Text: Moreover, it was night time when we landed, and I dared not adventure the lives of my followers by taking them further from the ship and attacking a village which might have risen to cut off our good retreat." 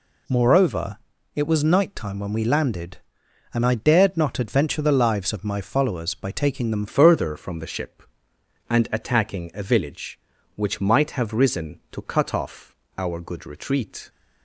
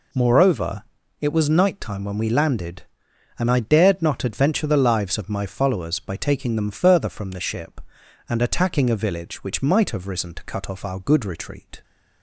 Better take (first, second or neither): second